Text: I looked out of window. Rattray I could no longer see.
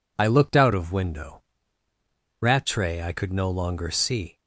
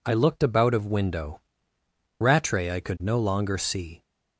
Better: first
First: none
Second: says "about" for "out"; at 0.4 s

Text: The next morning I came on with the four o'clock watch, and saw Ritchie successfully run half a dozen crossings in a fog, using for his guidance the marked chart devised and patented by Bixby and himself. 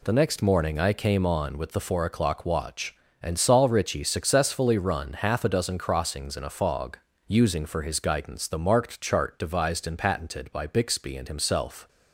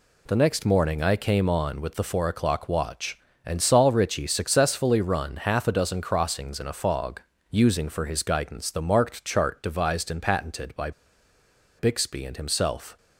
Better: first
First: none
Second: pauses between "by" and "Bixby"; noticeable; at 10.9 s; 0.87 s long

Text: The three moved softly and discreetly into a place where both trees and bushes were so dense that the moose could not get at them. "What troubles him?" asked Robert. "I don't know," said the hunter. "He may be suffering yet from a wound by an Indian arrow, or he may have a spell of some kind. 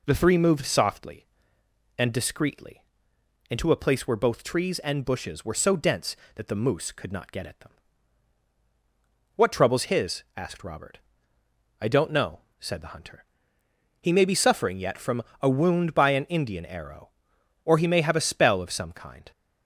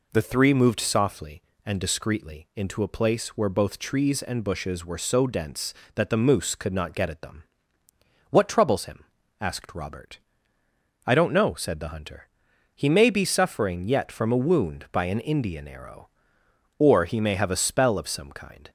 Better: second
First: pauses between "discreetly" and "into"; noticeable; at 2.8 s; 0.66 s long // says "his" for "him"; at 9.8 s // pauses between "from" and "a"; slight; at 15.2 s; 0.18 s long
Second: none

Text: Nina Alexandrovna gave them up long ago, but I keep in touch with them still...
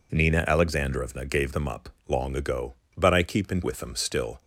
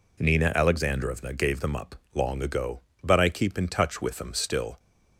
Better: second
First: pauses between "up" and "long"; slight; at 1.8 s; 0.20 s long // skips "touch"; at 3.6 s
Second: pauses between "up" and "long"; slight; at 1.9 s; 0.20 s long

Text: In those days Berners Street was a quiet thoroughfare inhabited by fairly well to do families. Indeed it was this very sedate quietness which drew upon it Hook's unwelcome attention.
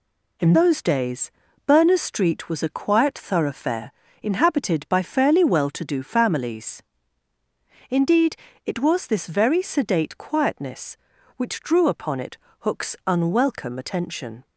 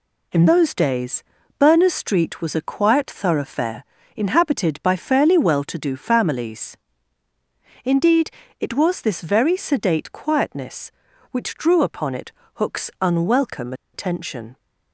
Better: first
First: pauses between "days" and "Berners"; slight; at 1.3 s; 0.34 s long // pauses between "thoroughfare" and "inhabited"; slight; at 3.9 s; 0.30 s long // pauses between "Indeed" and "it"; slight; at 8.3 s; 0.30 s long // pauses between "it" and "Hook's"; slight; at 12.3 s; 0.22 s long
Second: pauses between "days" and "Berners"; slight; at 1.2 s; 0.34 s long // pauses between "thoroughfare" and "inhabited"; slight; at 3.8 s; 0.32 s long // pauses between "Indeed" and "it"; slight; at 8.2 s; 0.30 s long // pauses between "it" and "Hook's"; slight; at 12.3 s; 0.22 s long // pauses between "unwelcome" and "attention"; slight; at 13.7 s; 0.20 s long

